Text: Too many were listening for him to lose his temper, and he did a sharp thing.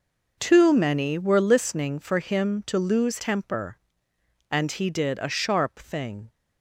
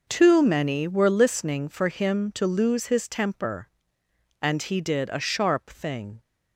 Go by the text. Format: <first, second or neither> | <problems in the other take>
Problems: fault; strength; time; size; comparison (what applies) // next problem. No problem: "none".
second | skips "his"; at 3.1 s